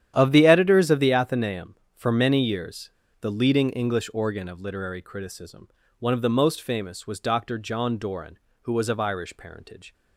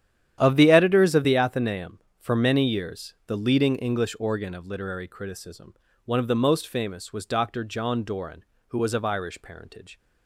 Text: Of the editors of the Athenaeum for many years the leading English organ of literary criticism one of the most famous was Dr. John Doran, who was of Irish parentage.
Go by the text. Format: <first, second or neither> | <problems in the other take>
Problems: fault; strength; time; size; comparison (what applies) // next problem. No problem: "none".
second | starts louder than the rest; strong; until 1.1 s; 10.5 dB; strong in the second // pauses between "years" and "the"; slight; at 2.8 s; 0.32 s long // pauses between "criticism" and "one"; slight; at 5.6 s; 0.30 s long; slight in the second